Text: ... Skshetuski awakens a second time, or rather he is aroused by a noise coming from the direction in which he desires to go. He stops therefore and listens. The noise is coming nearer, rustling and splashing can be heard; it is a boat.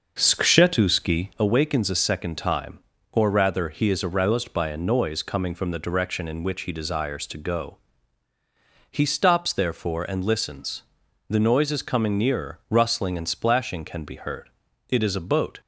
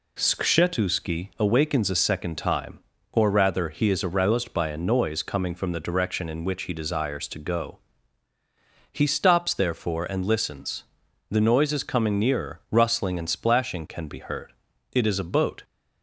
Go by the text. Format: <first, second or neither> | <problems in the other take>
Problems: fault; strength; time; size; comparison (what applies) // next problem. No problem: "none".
second | starts louder than the rest; noticeable; until 1.5 s; 6 dB